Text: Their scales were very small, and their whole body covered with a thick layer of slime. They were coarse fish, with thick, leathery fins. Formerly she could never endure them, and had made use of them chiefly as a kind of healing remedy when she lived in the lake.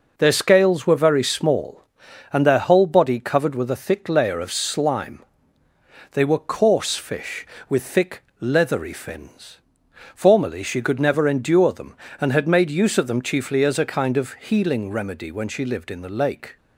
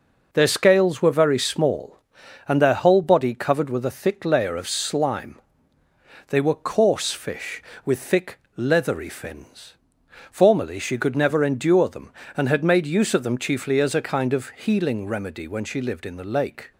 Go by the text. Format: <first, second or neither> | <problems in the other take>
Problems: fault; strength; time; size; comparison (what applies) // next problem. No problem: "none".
neither | none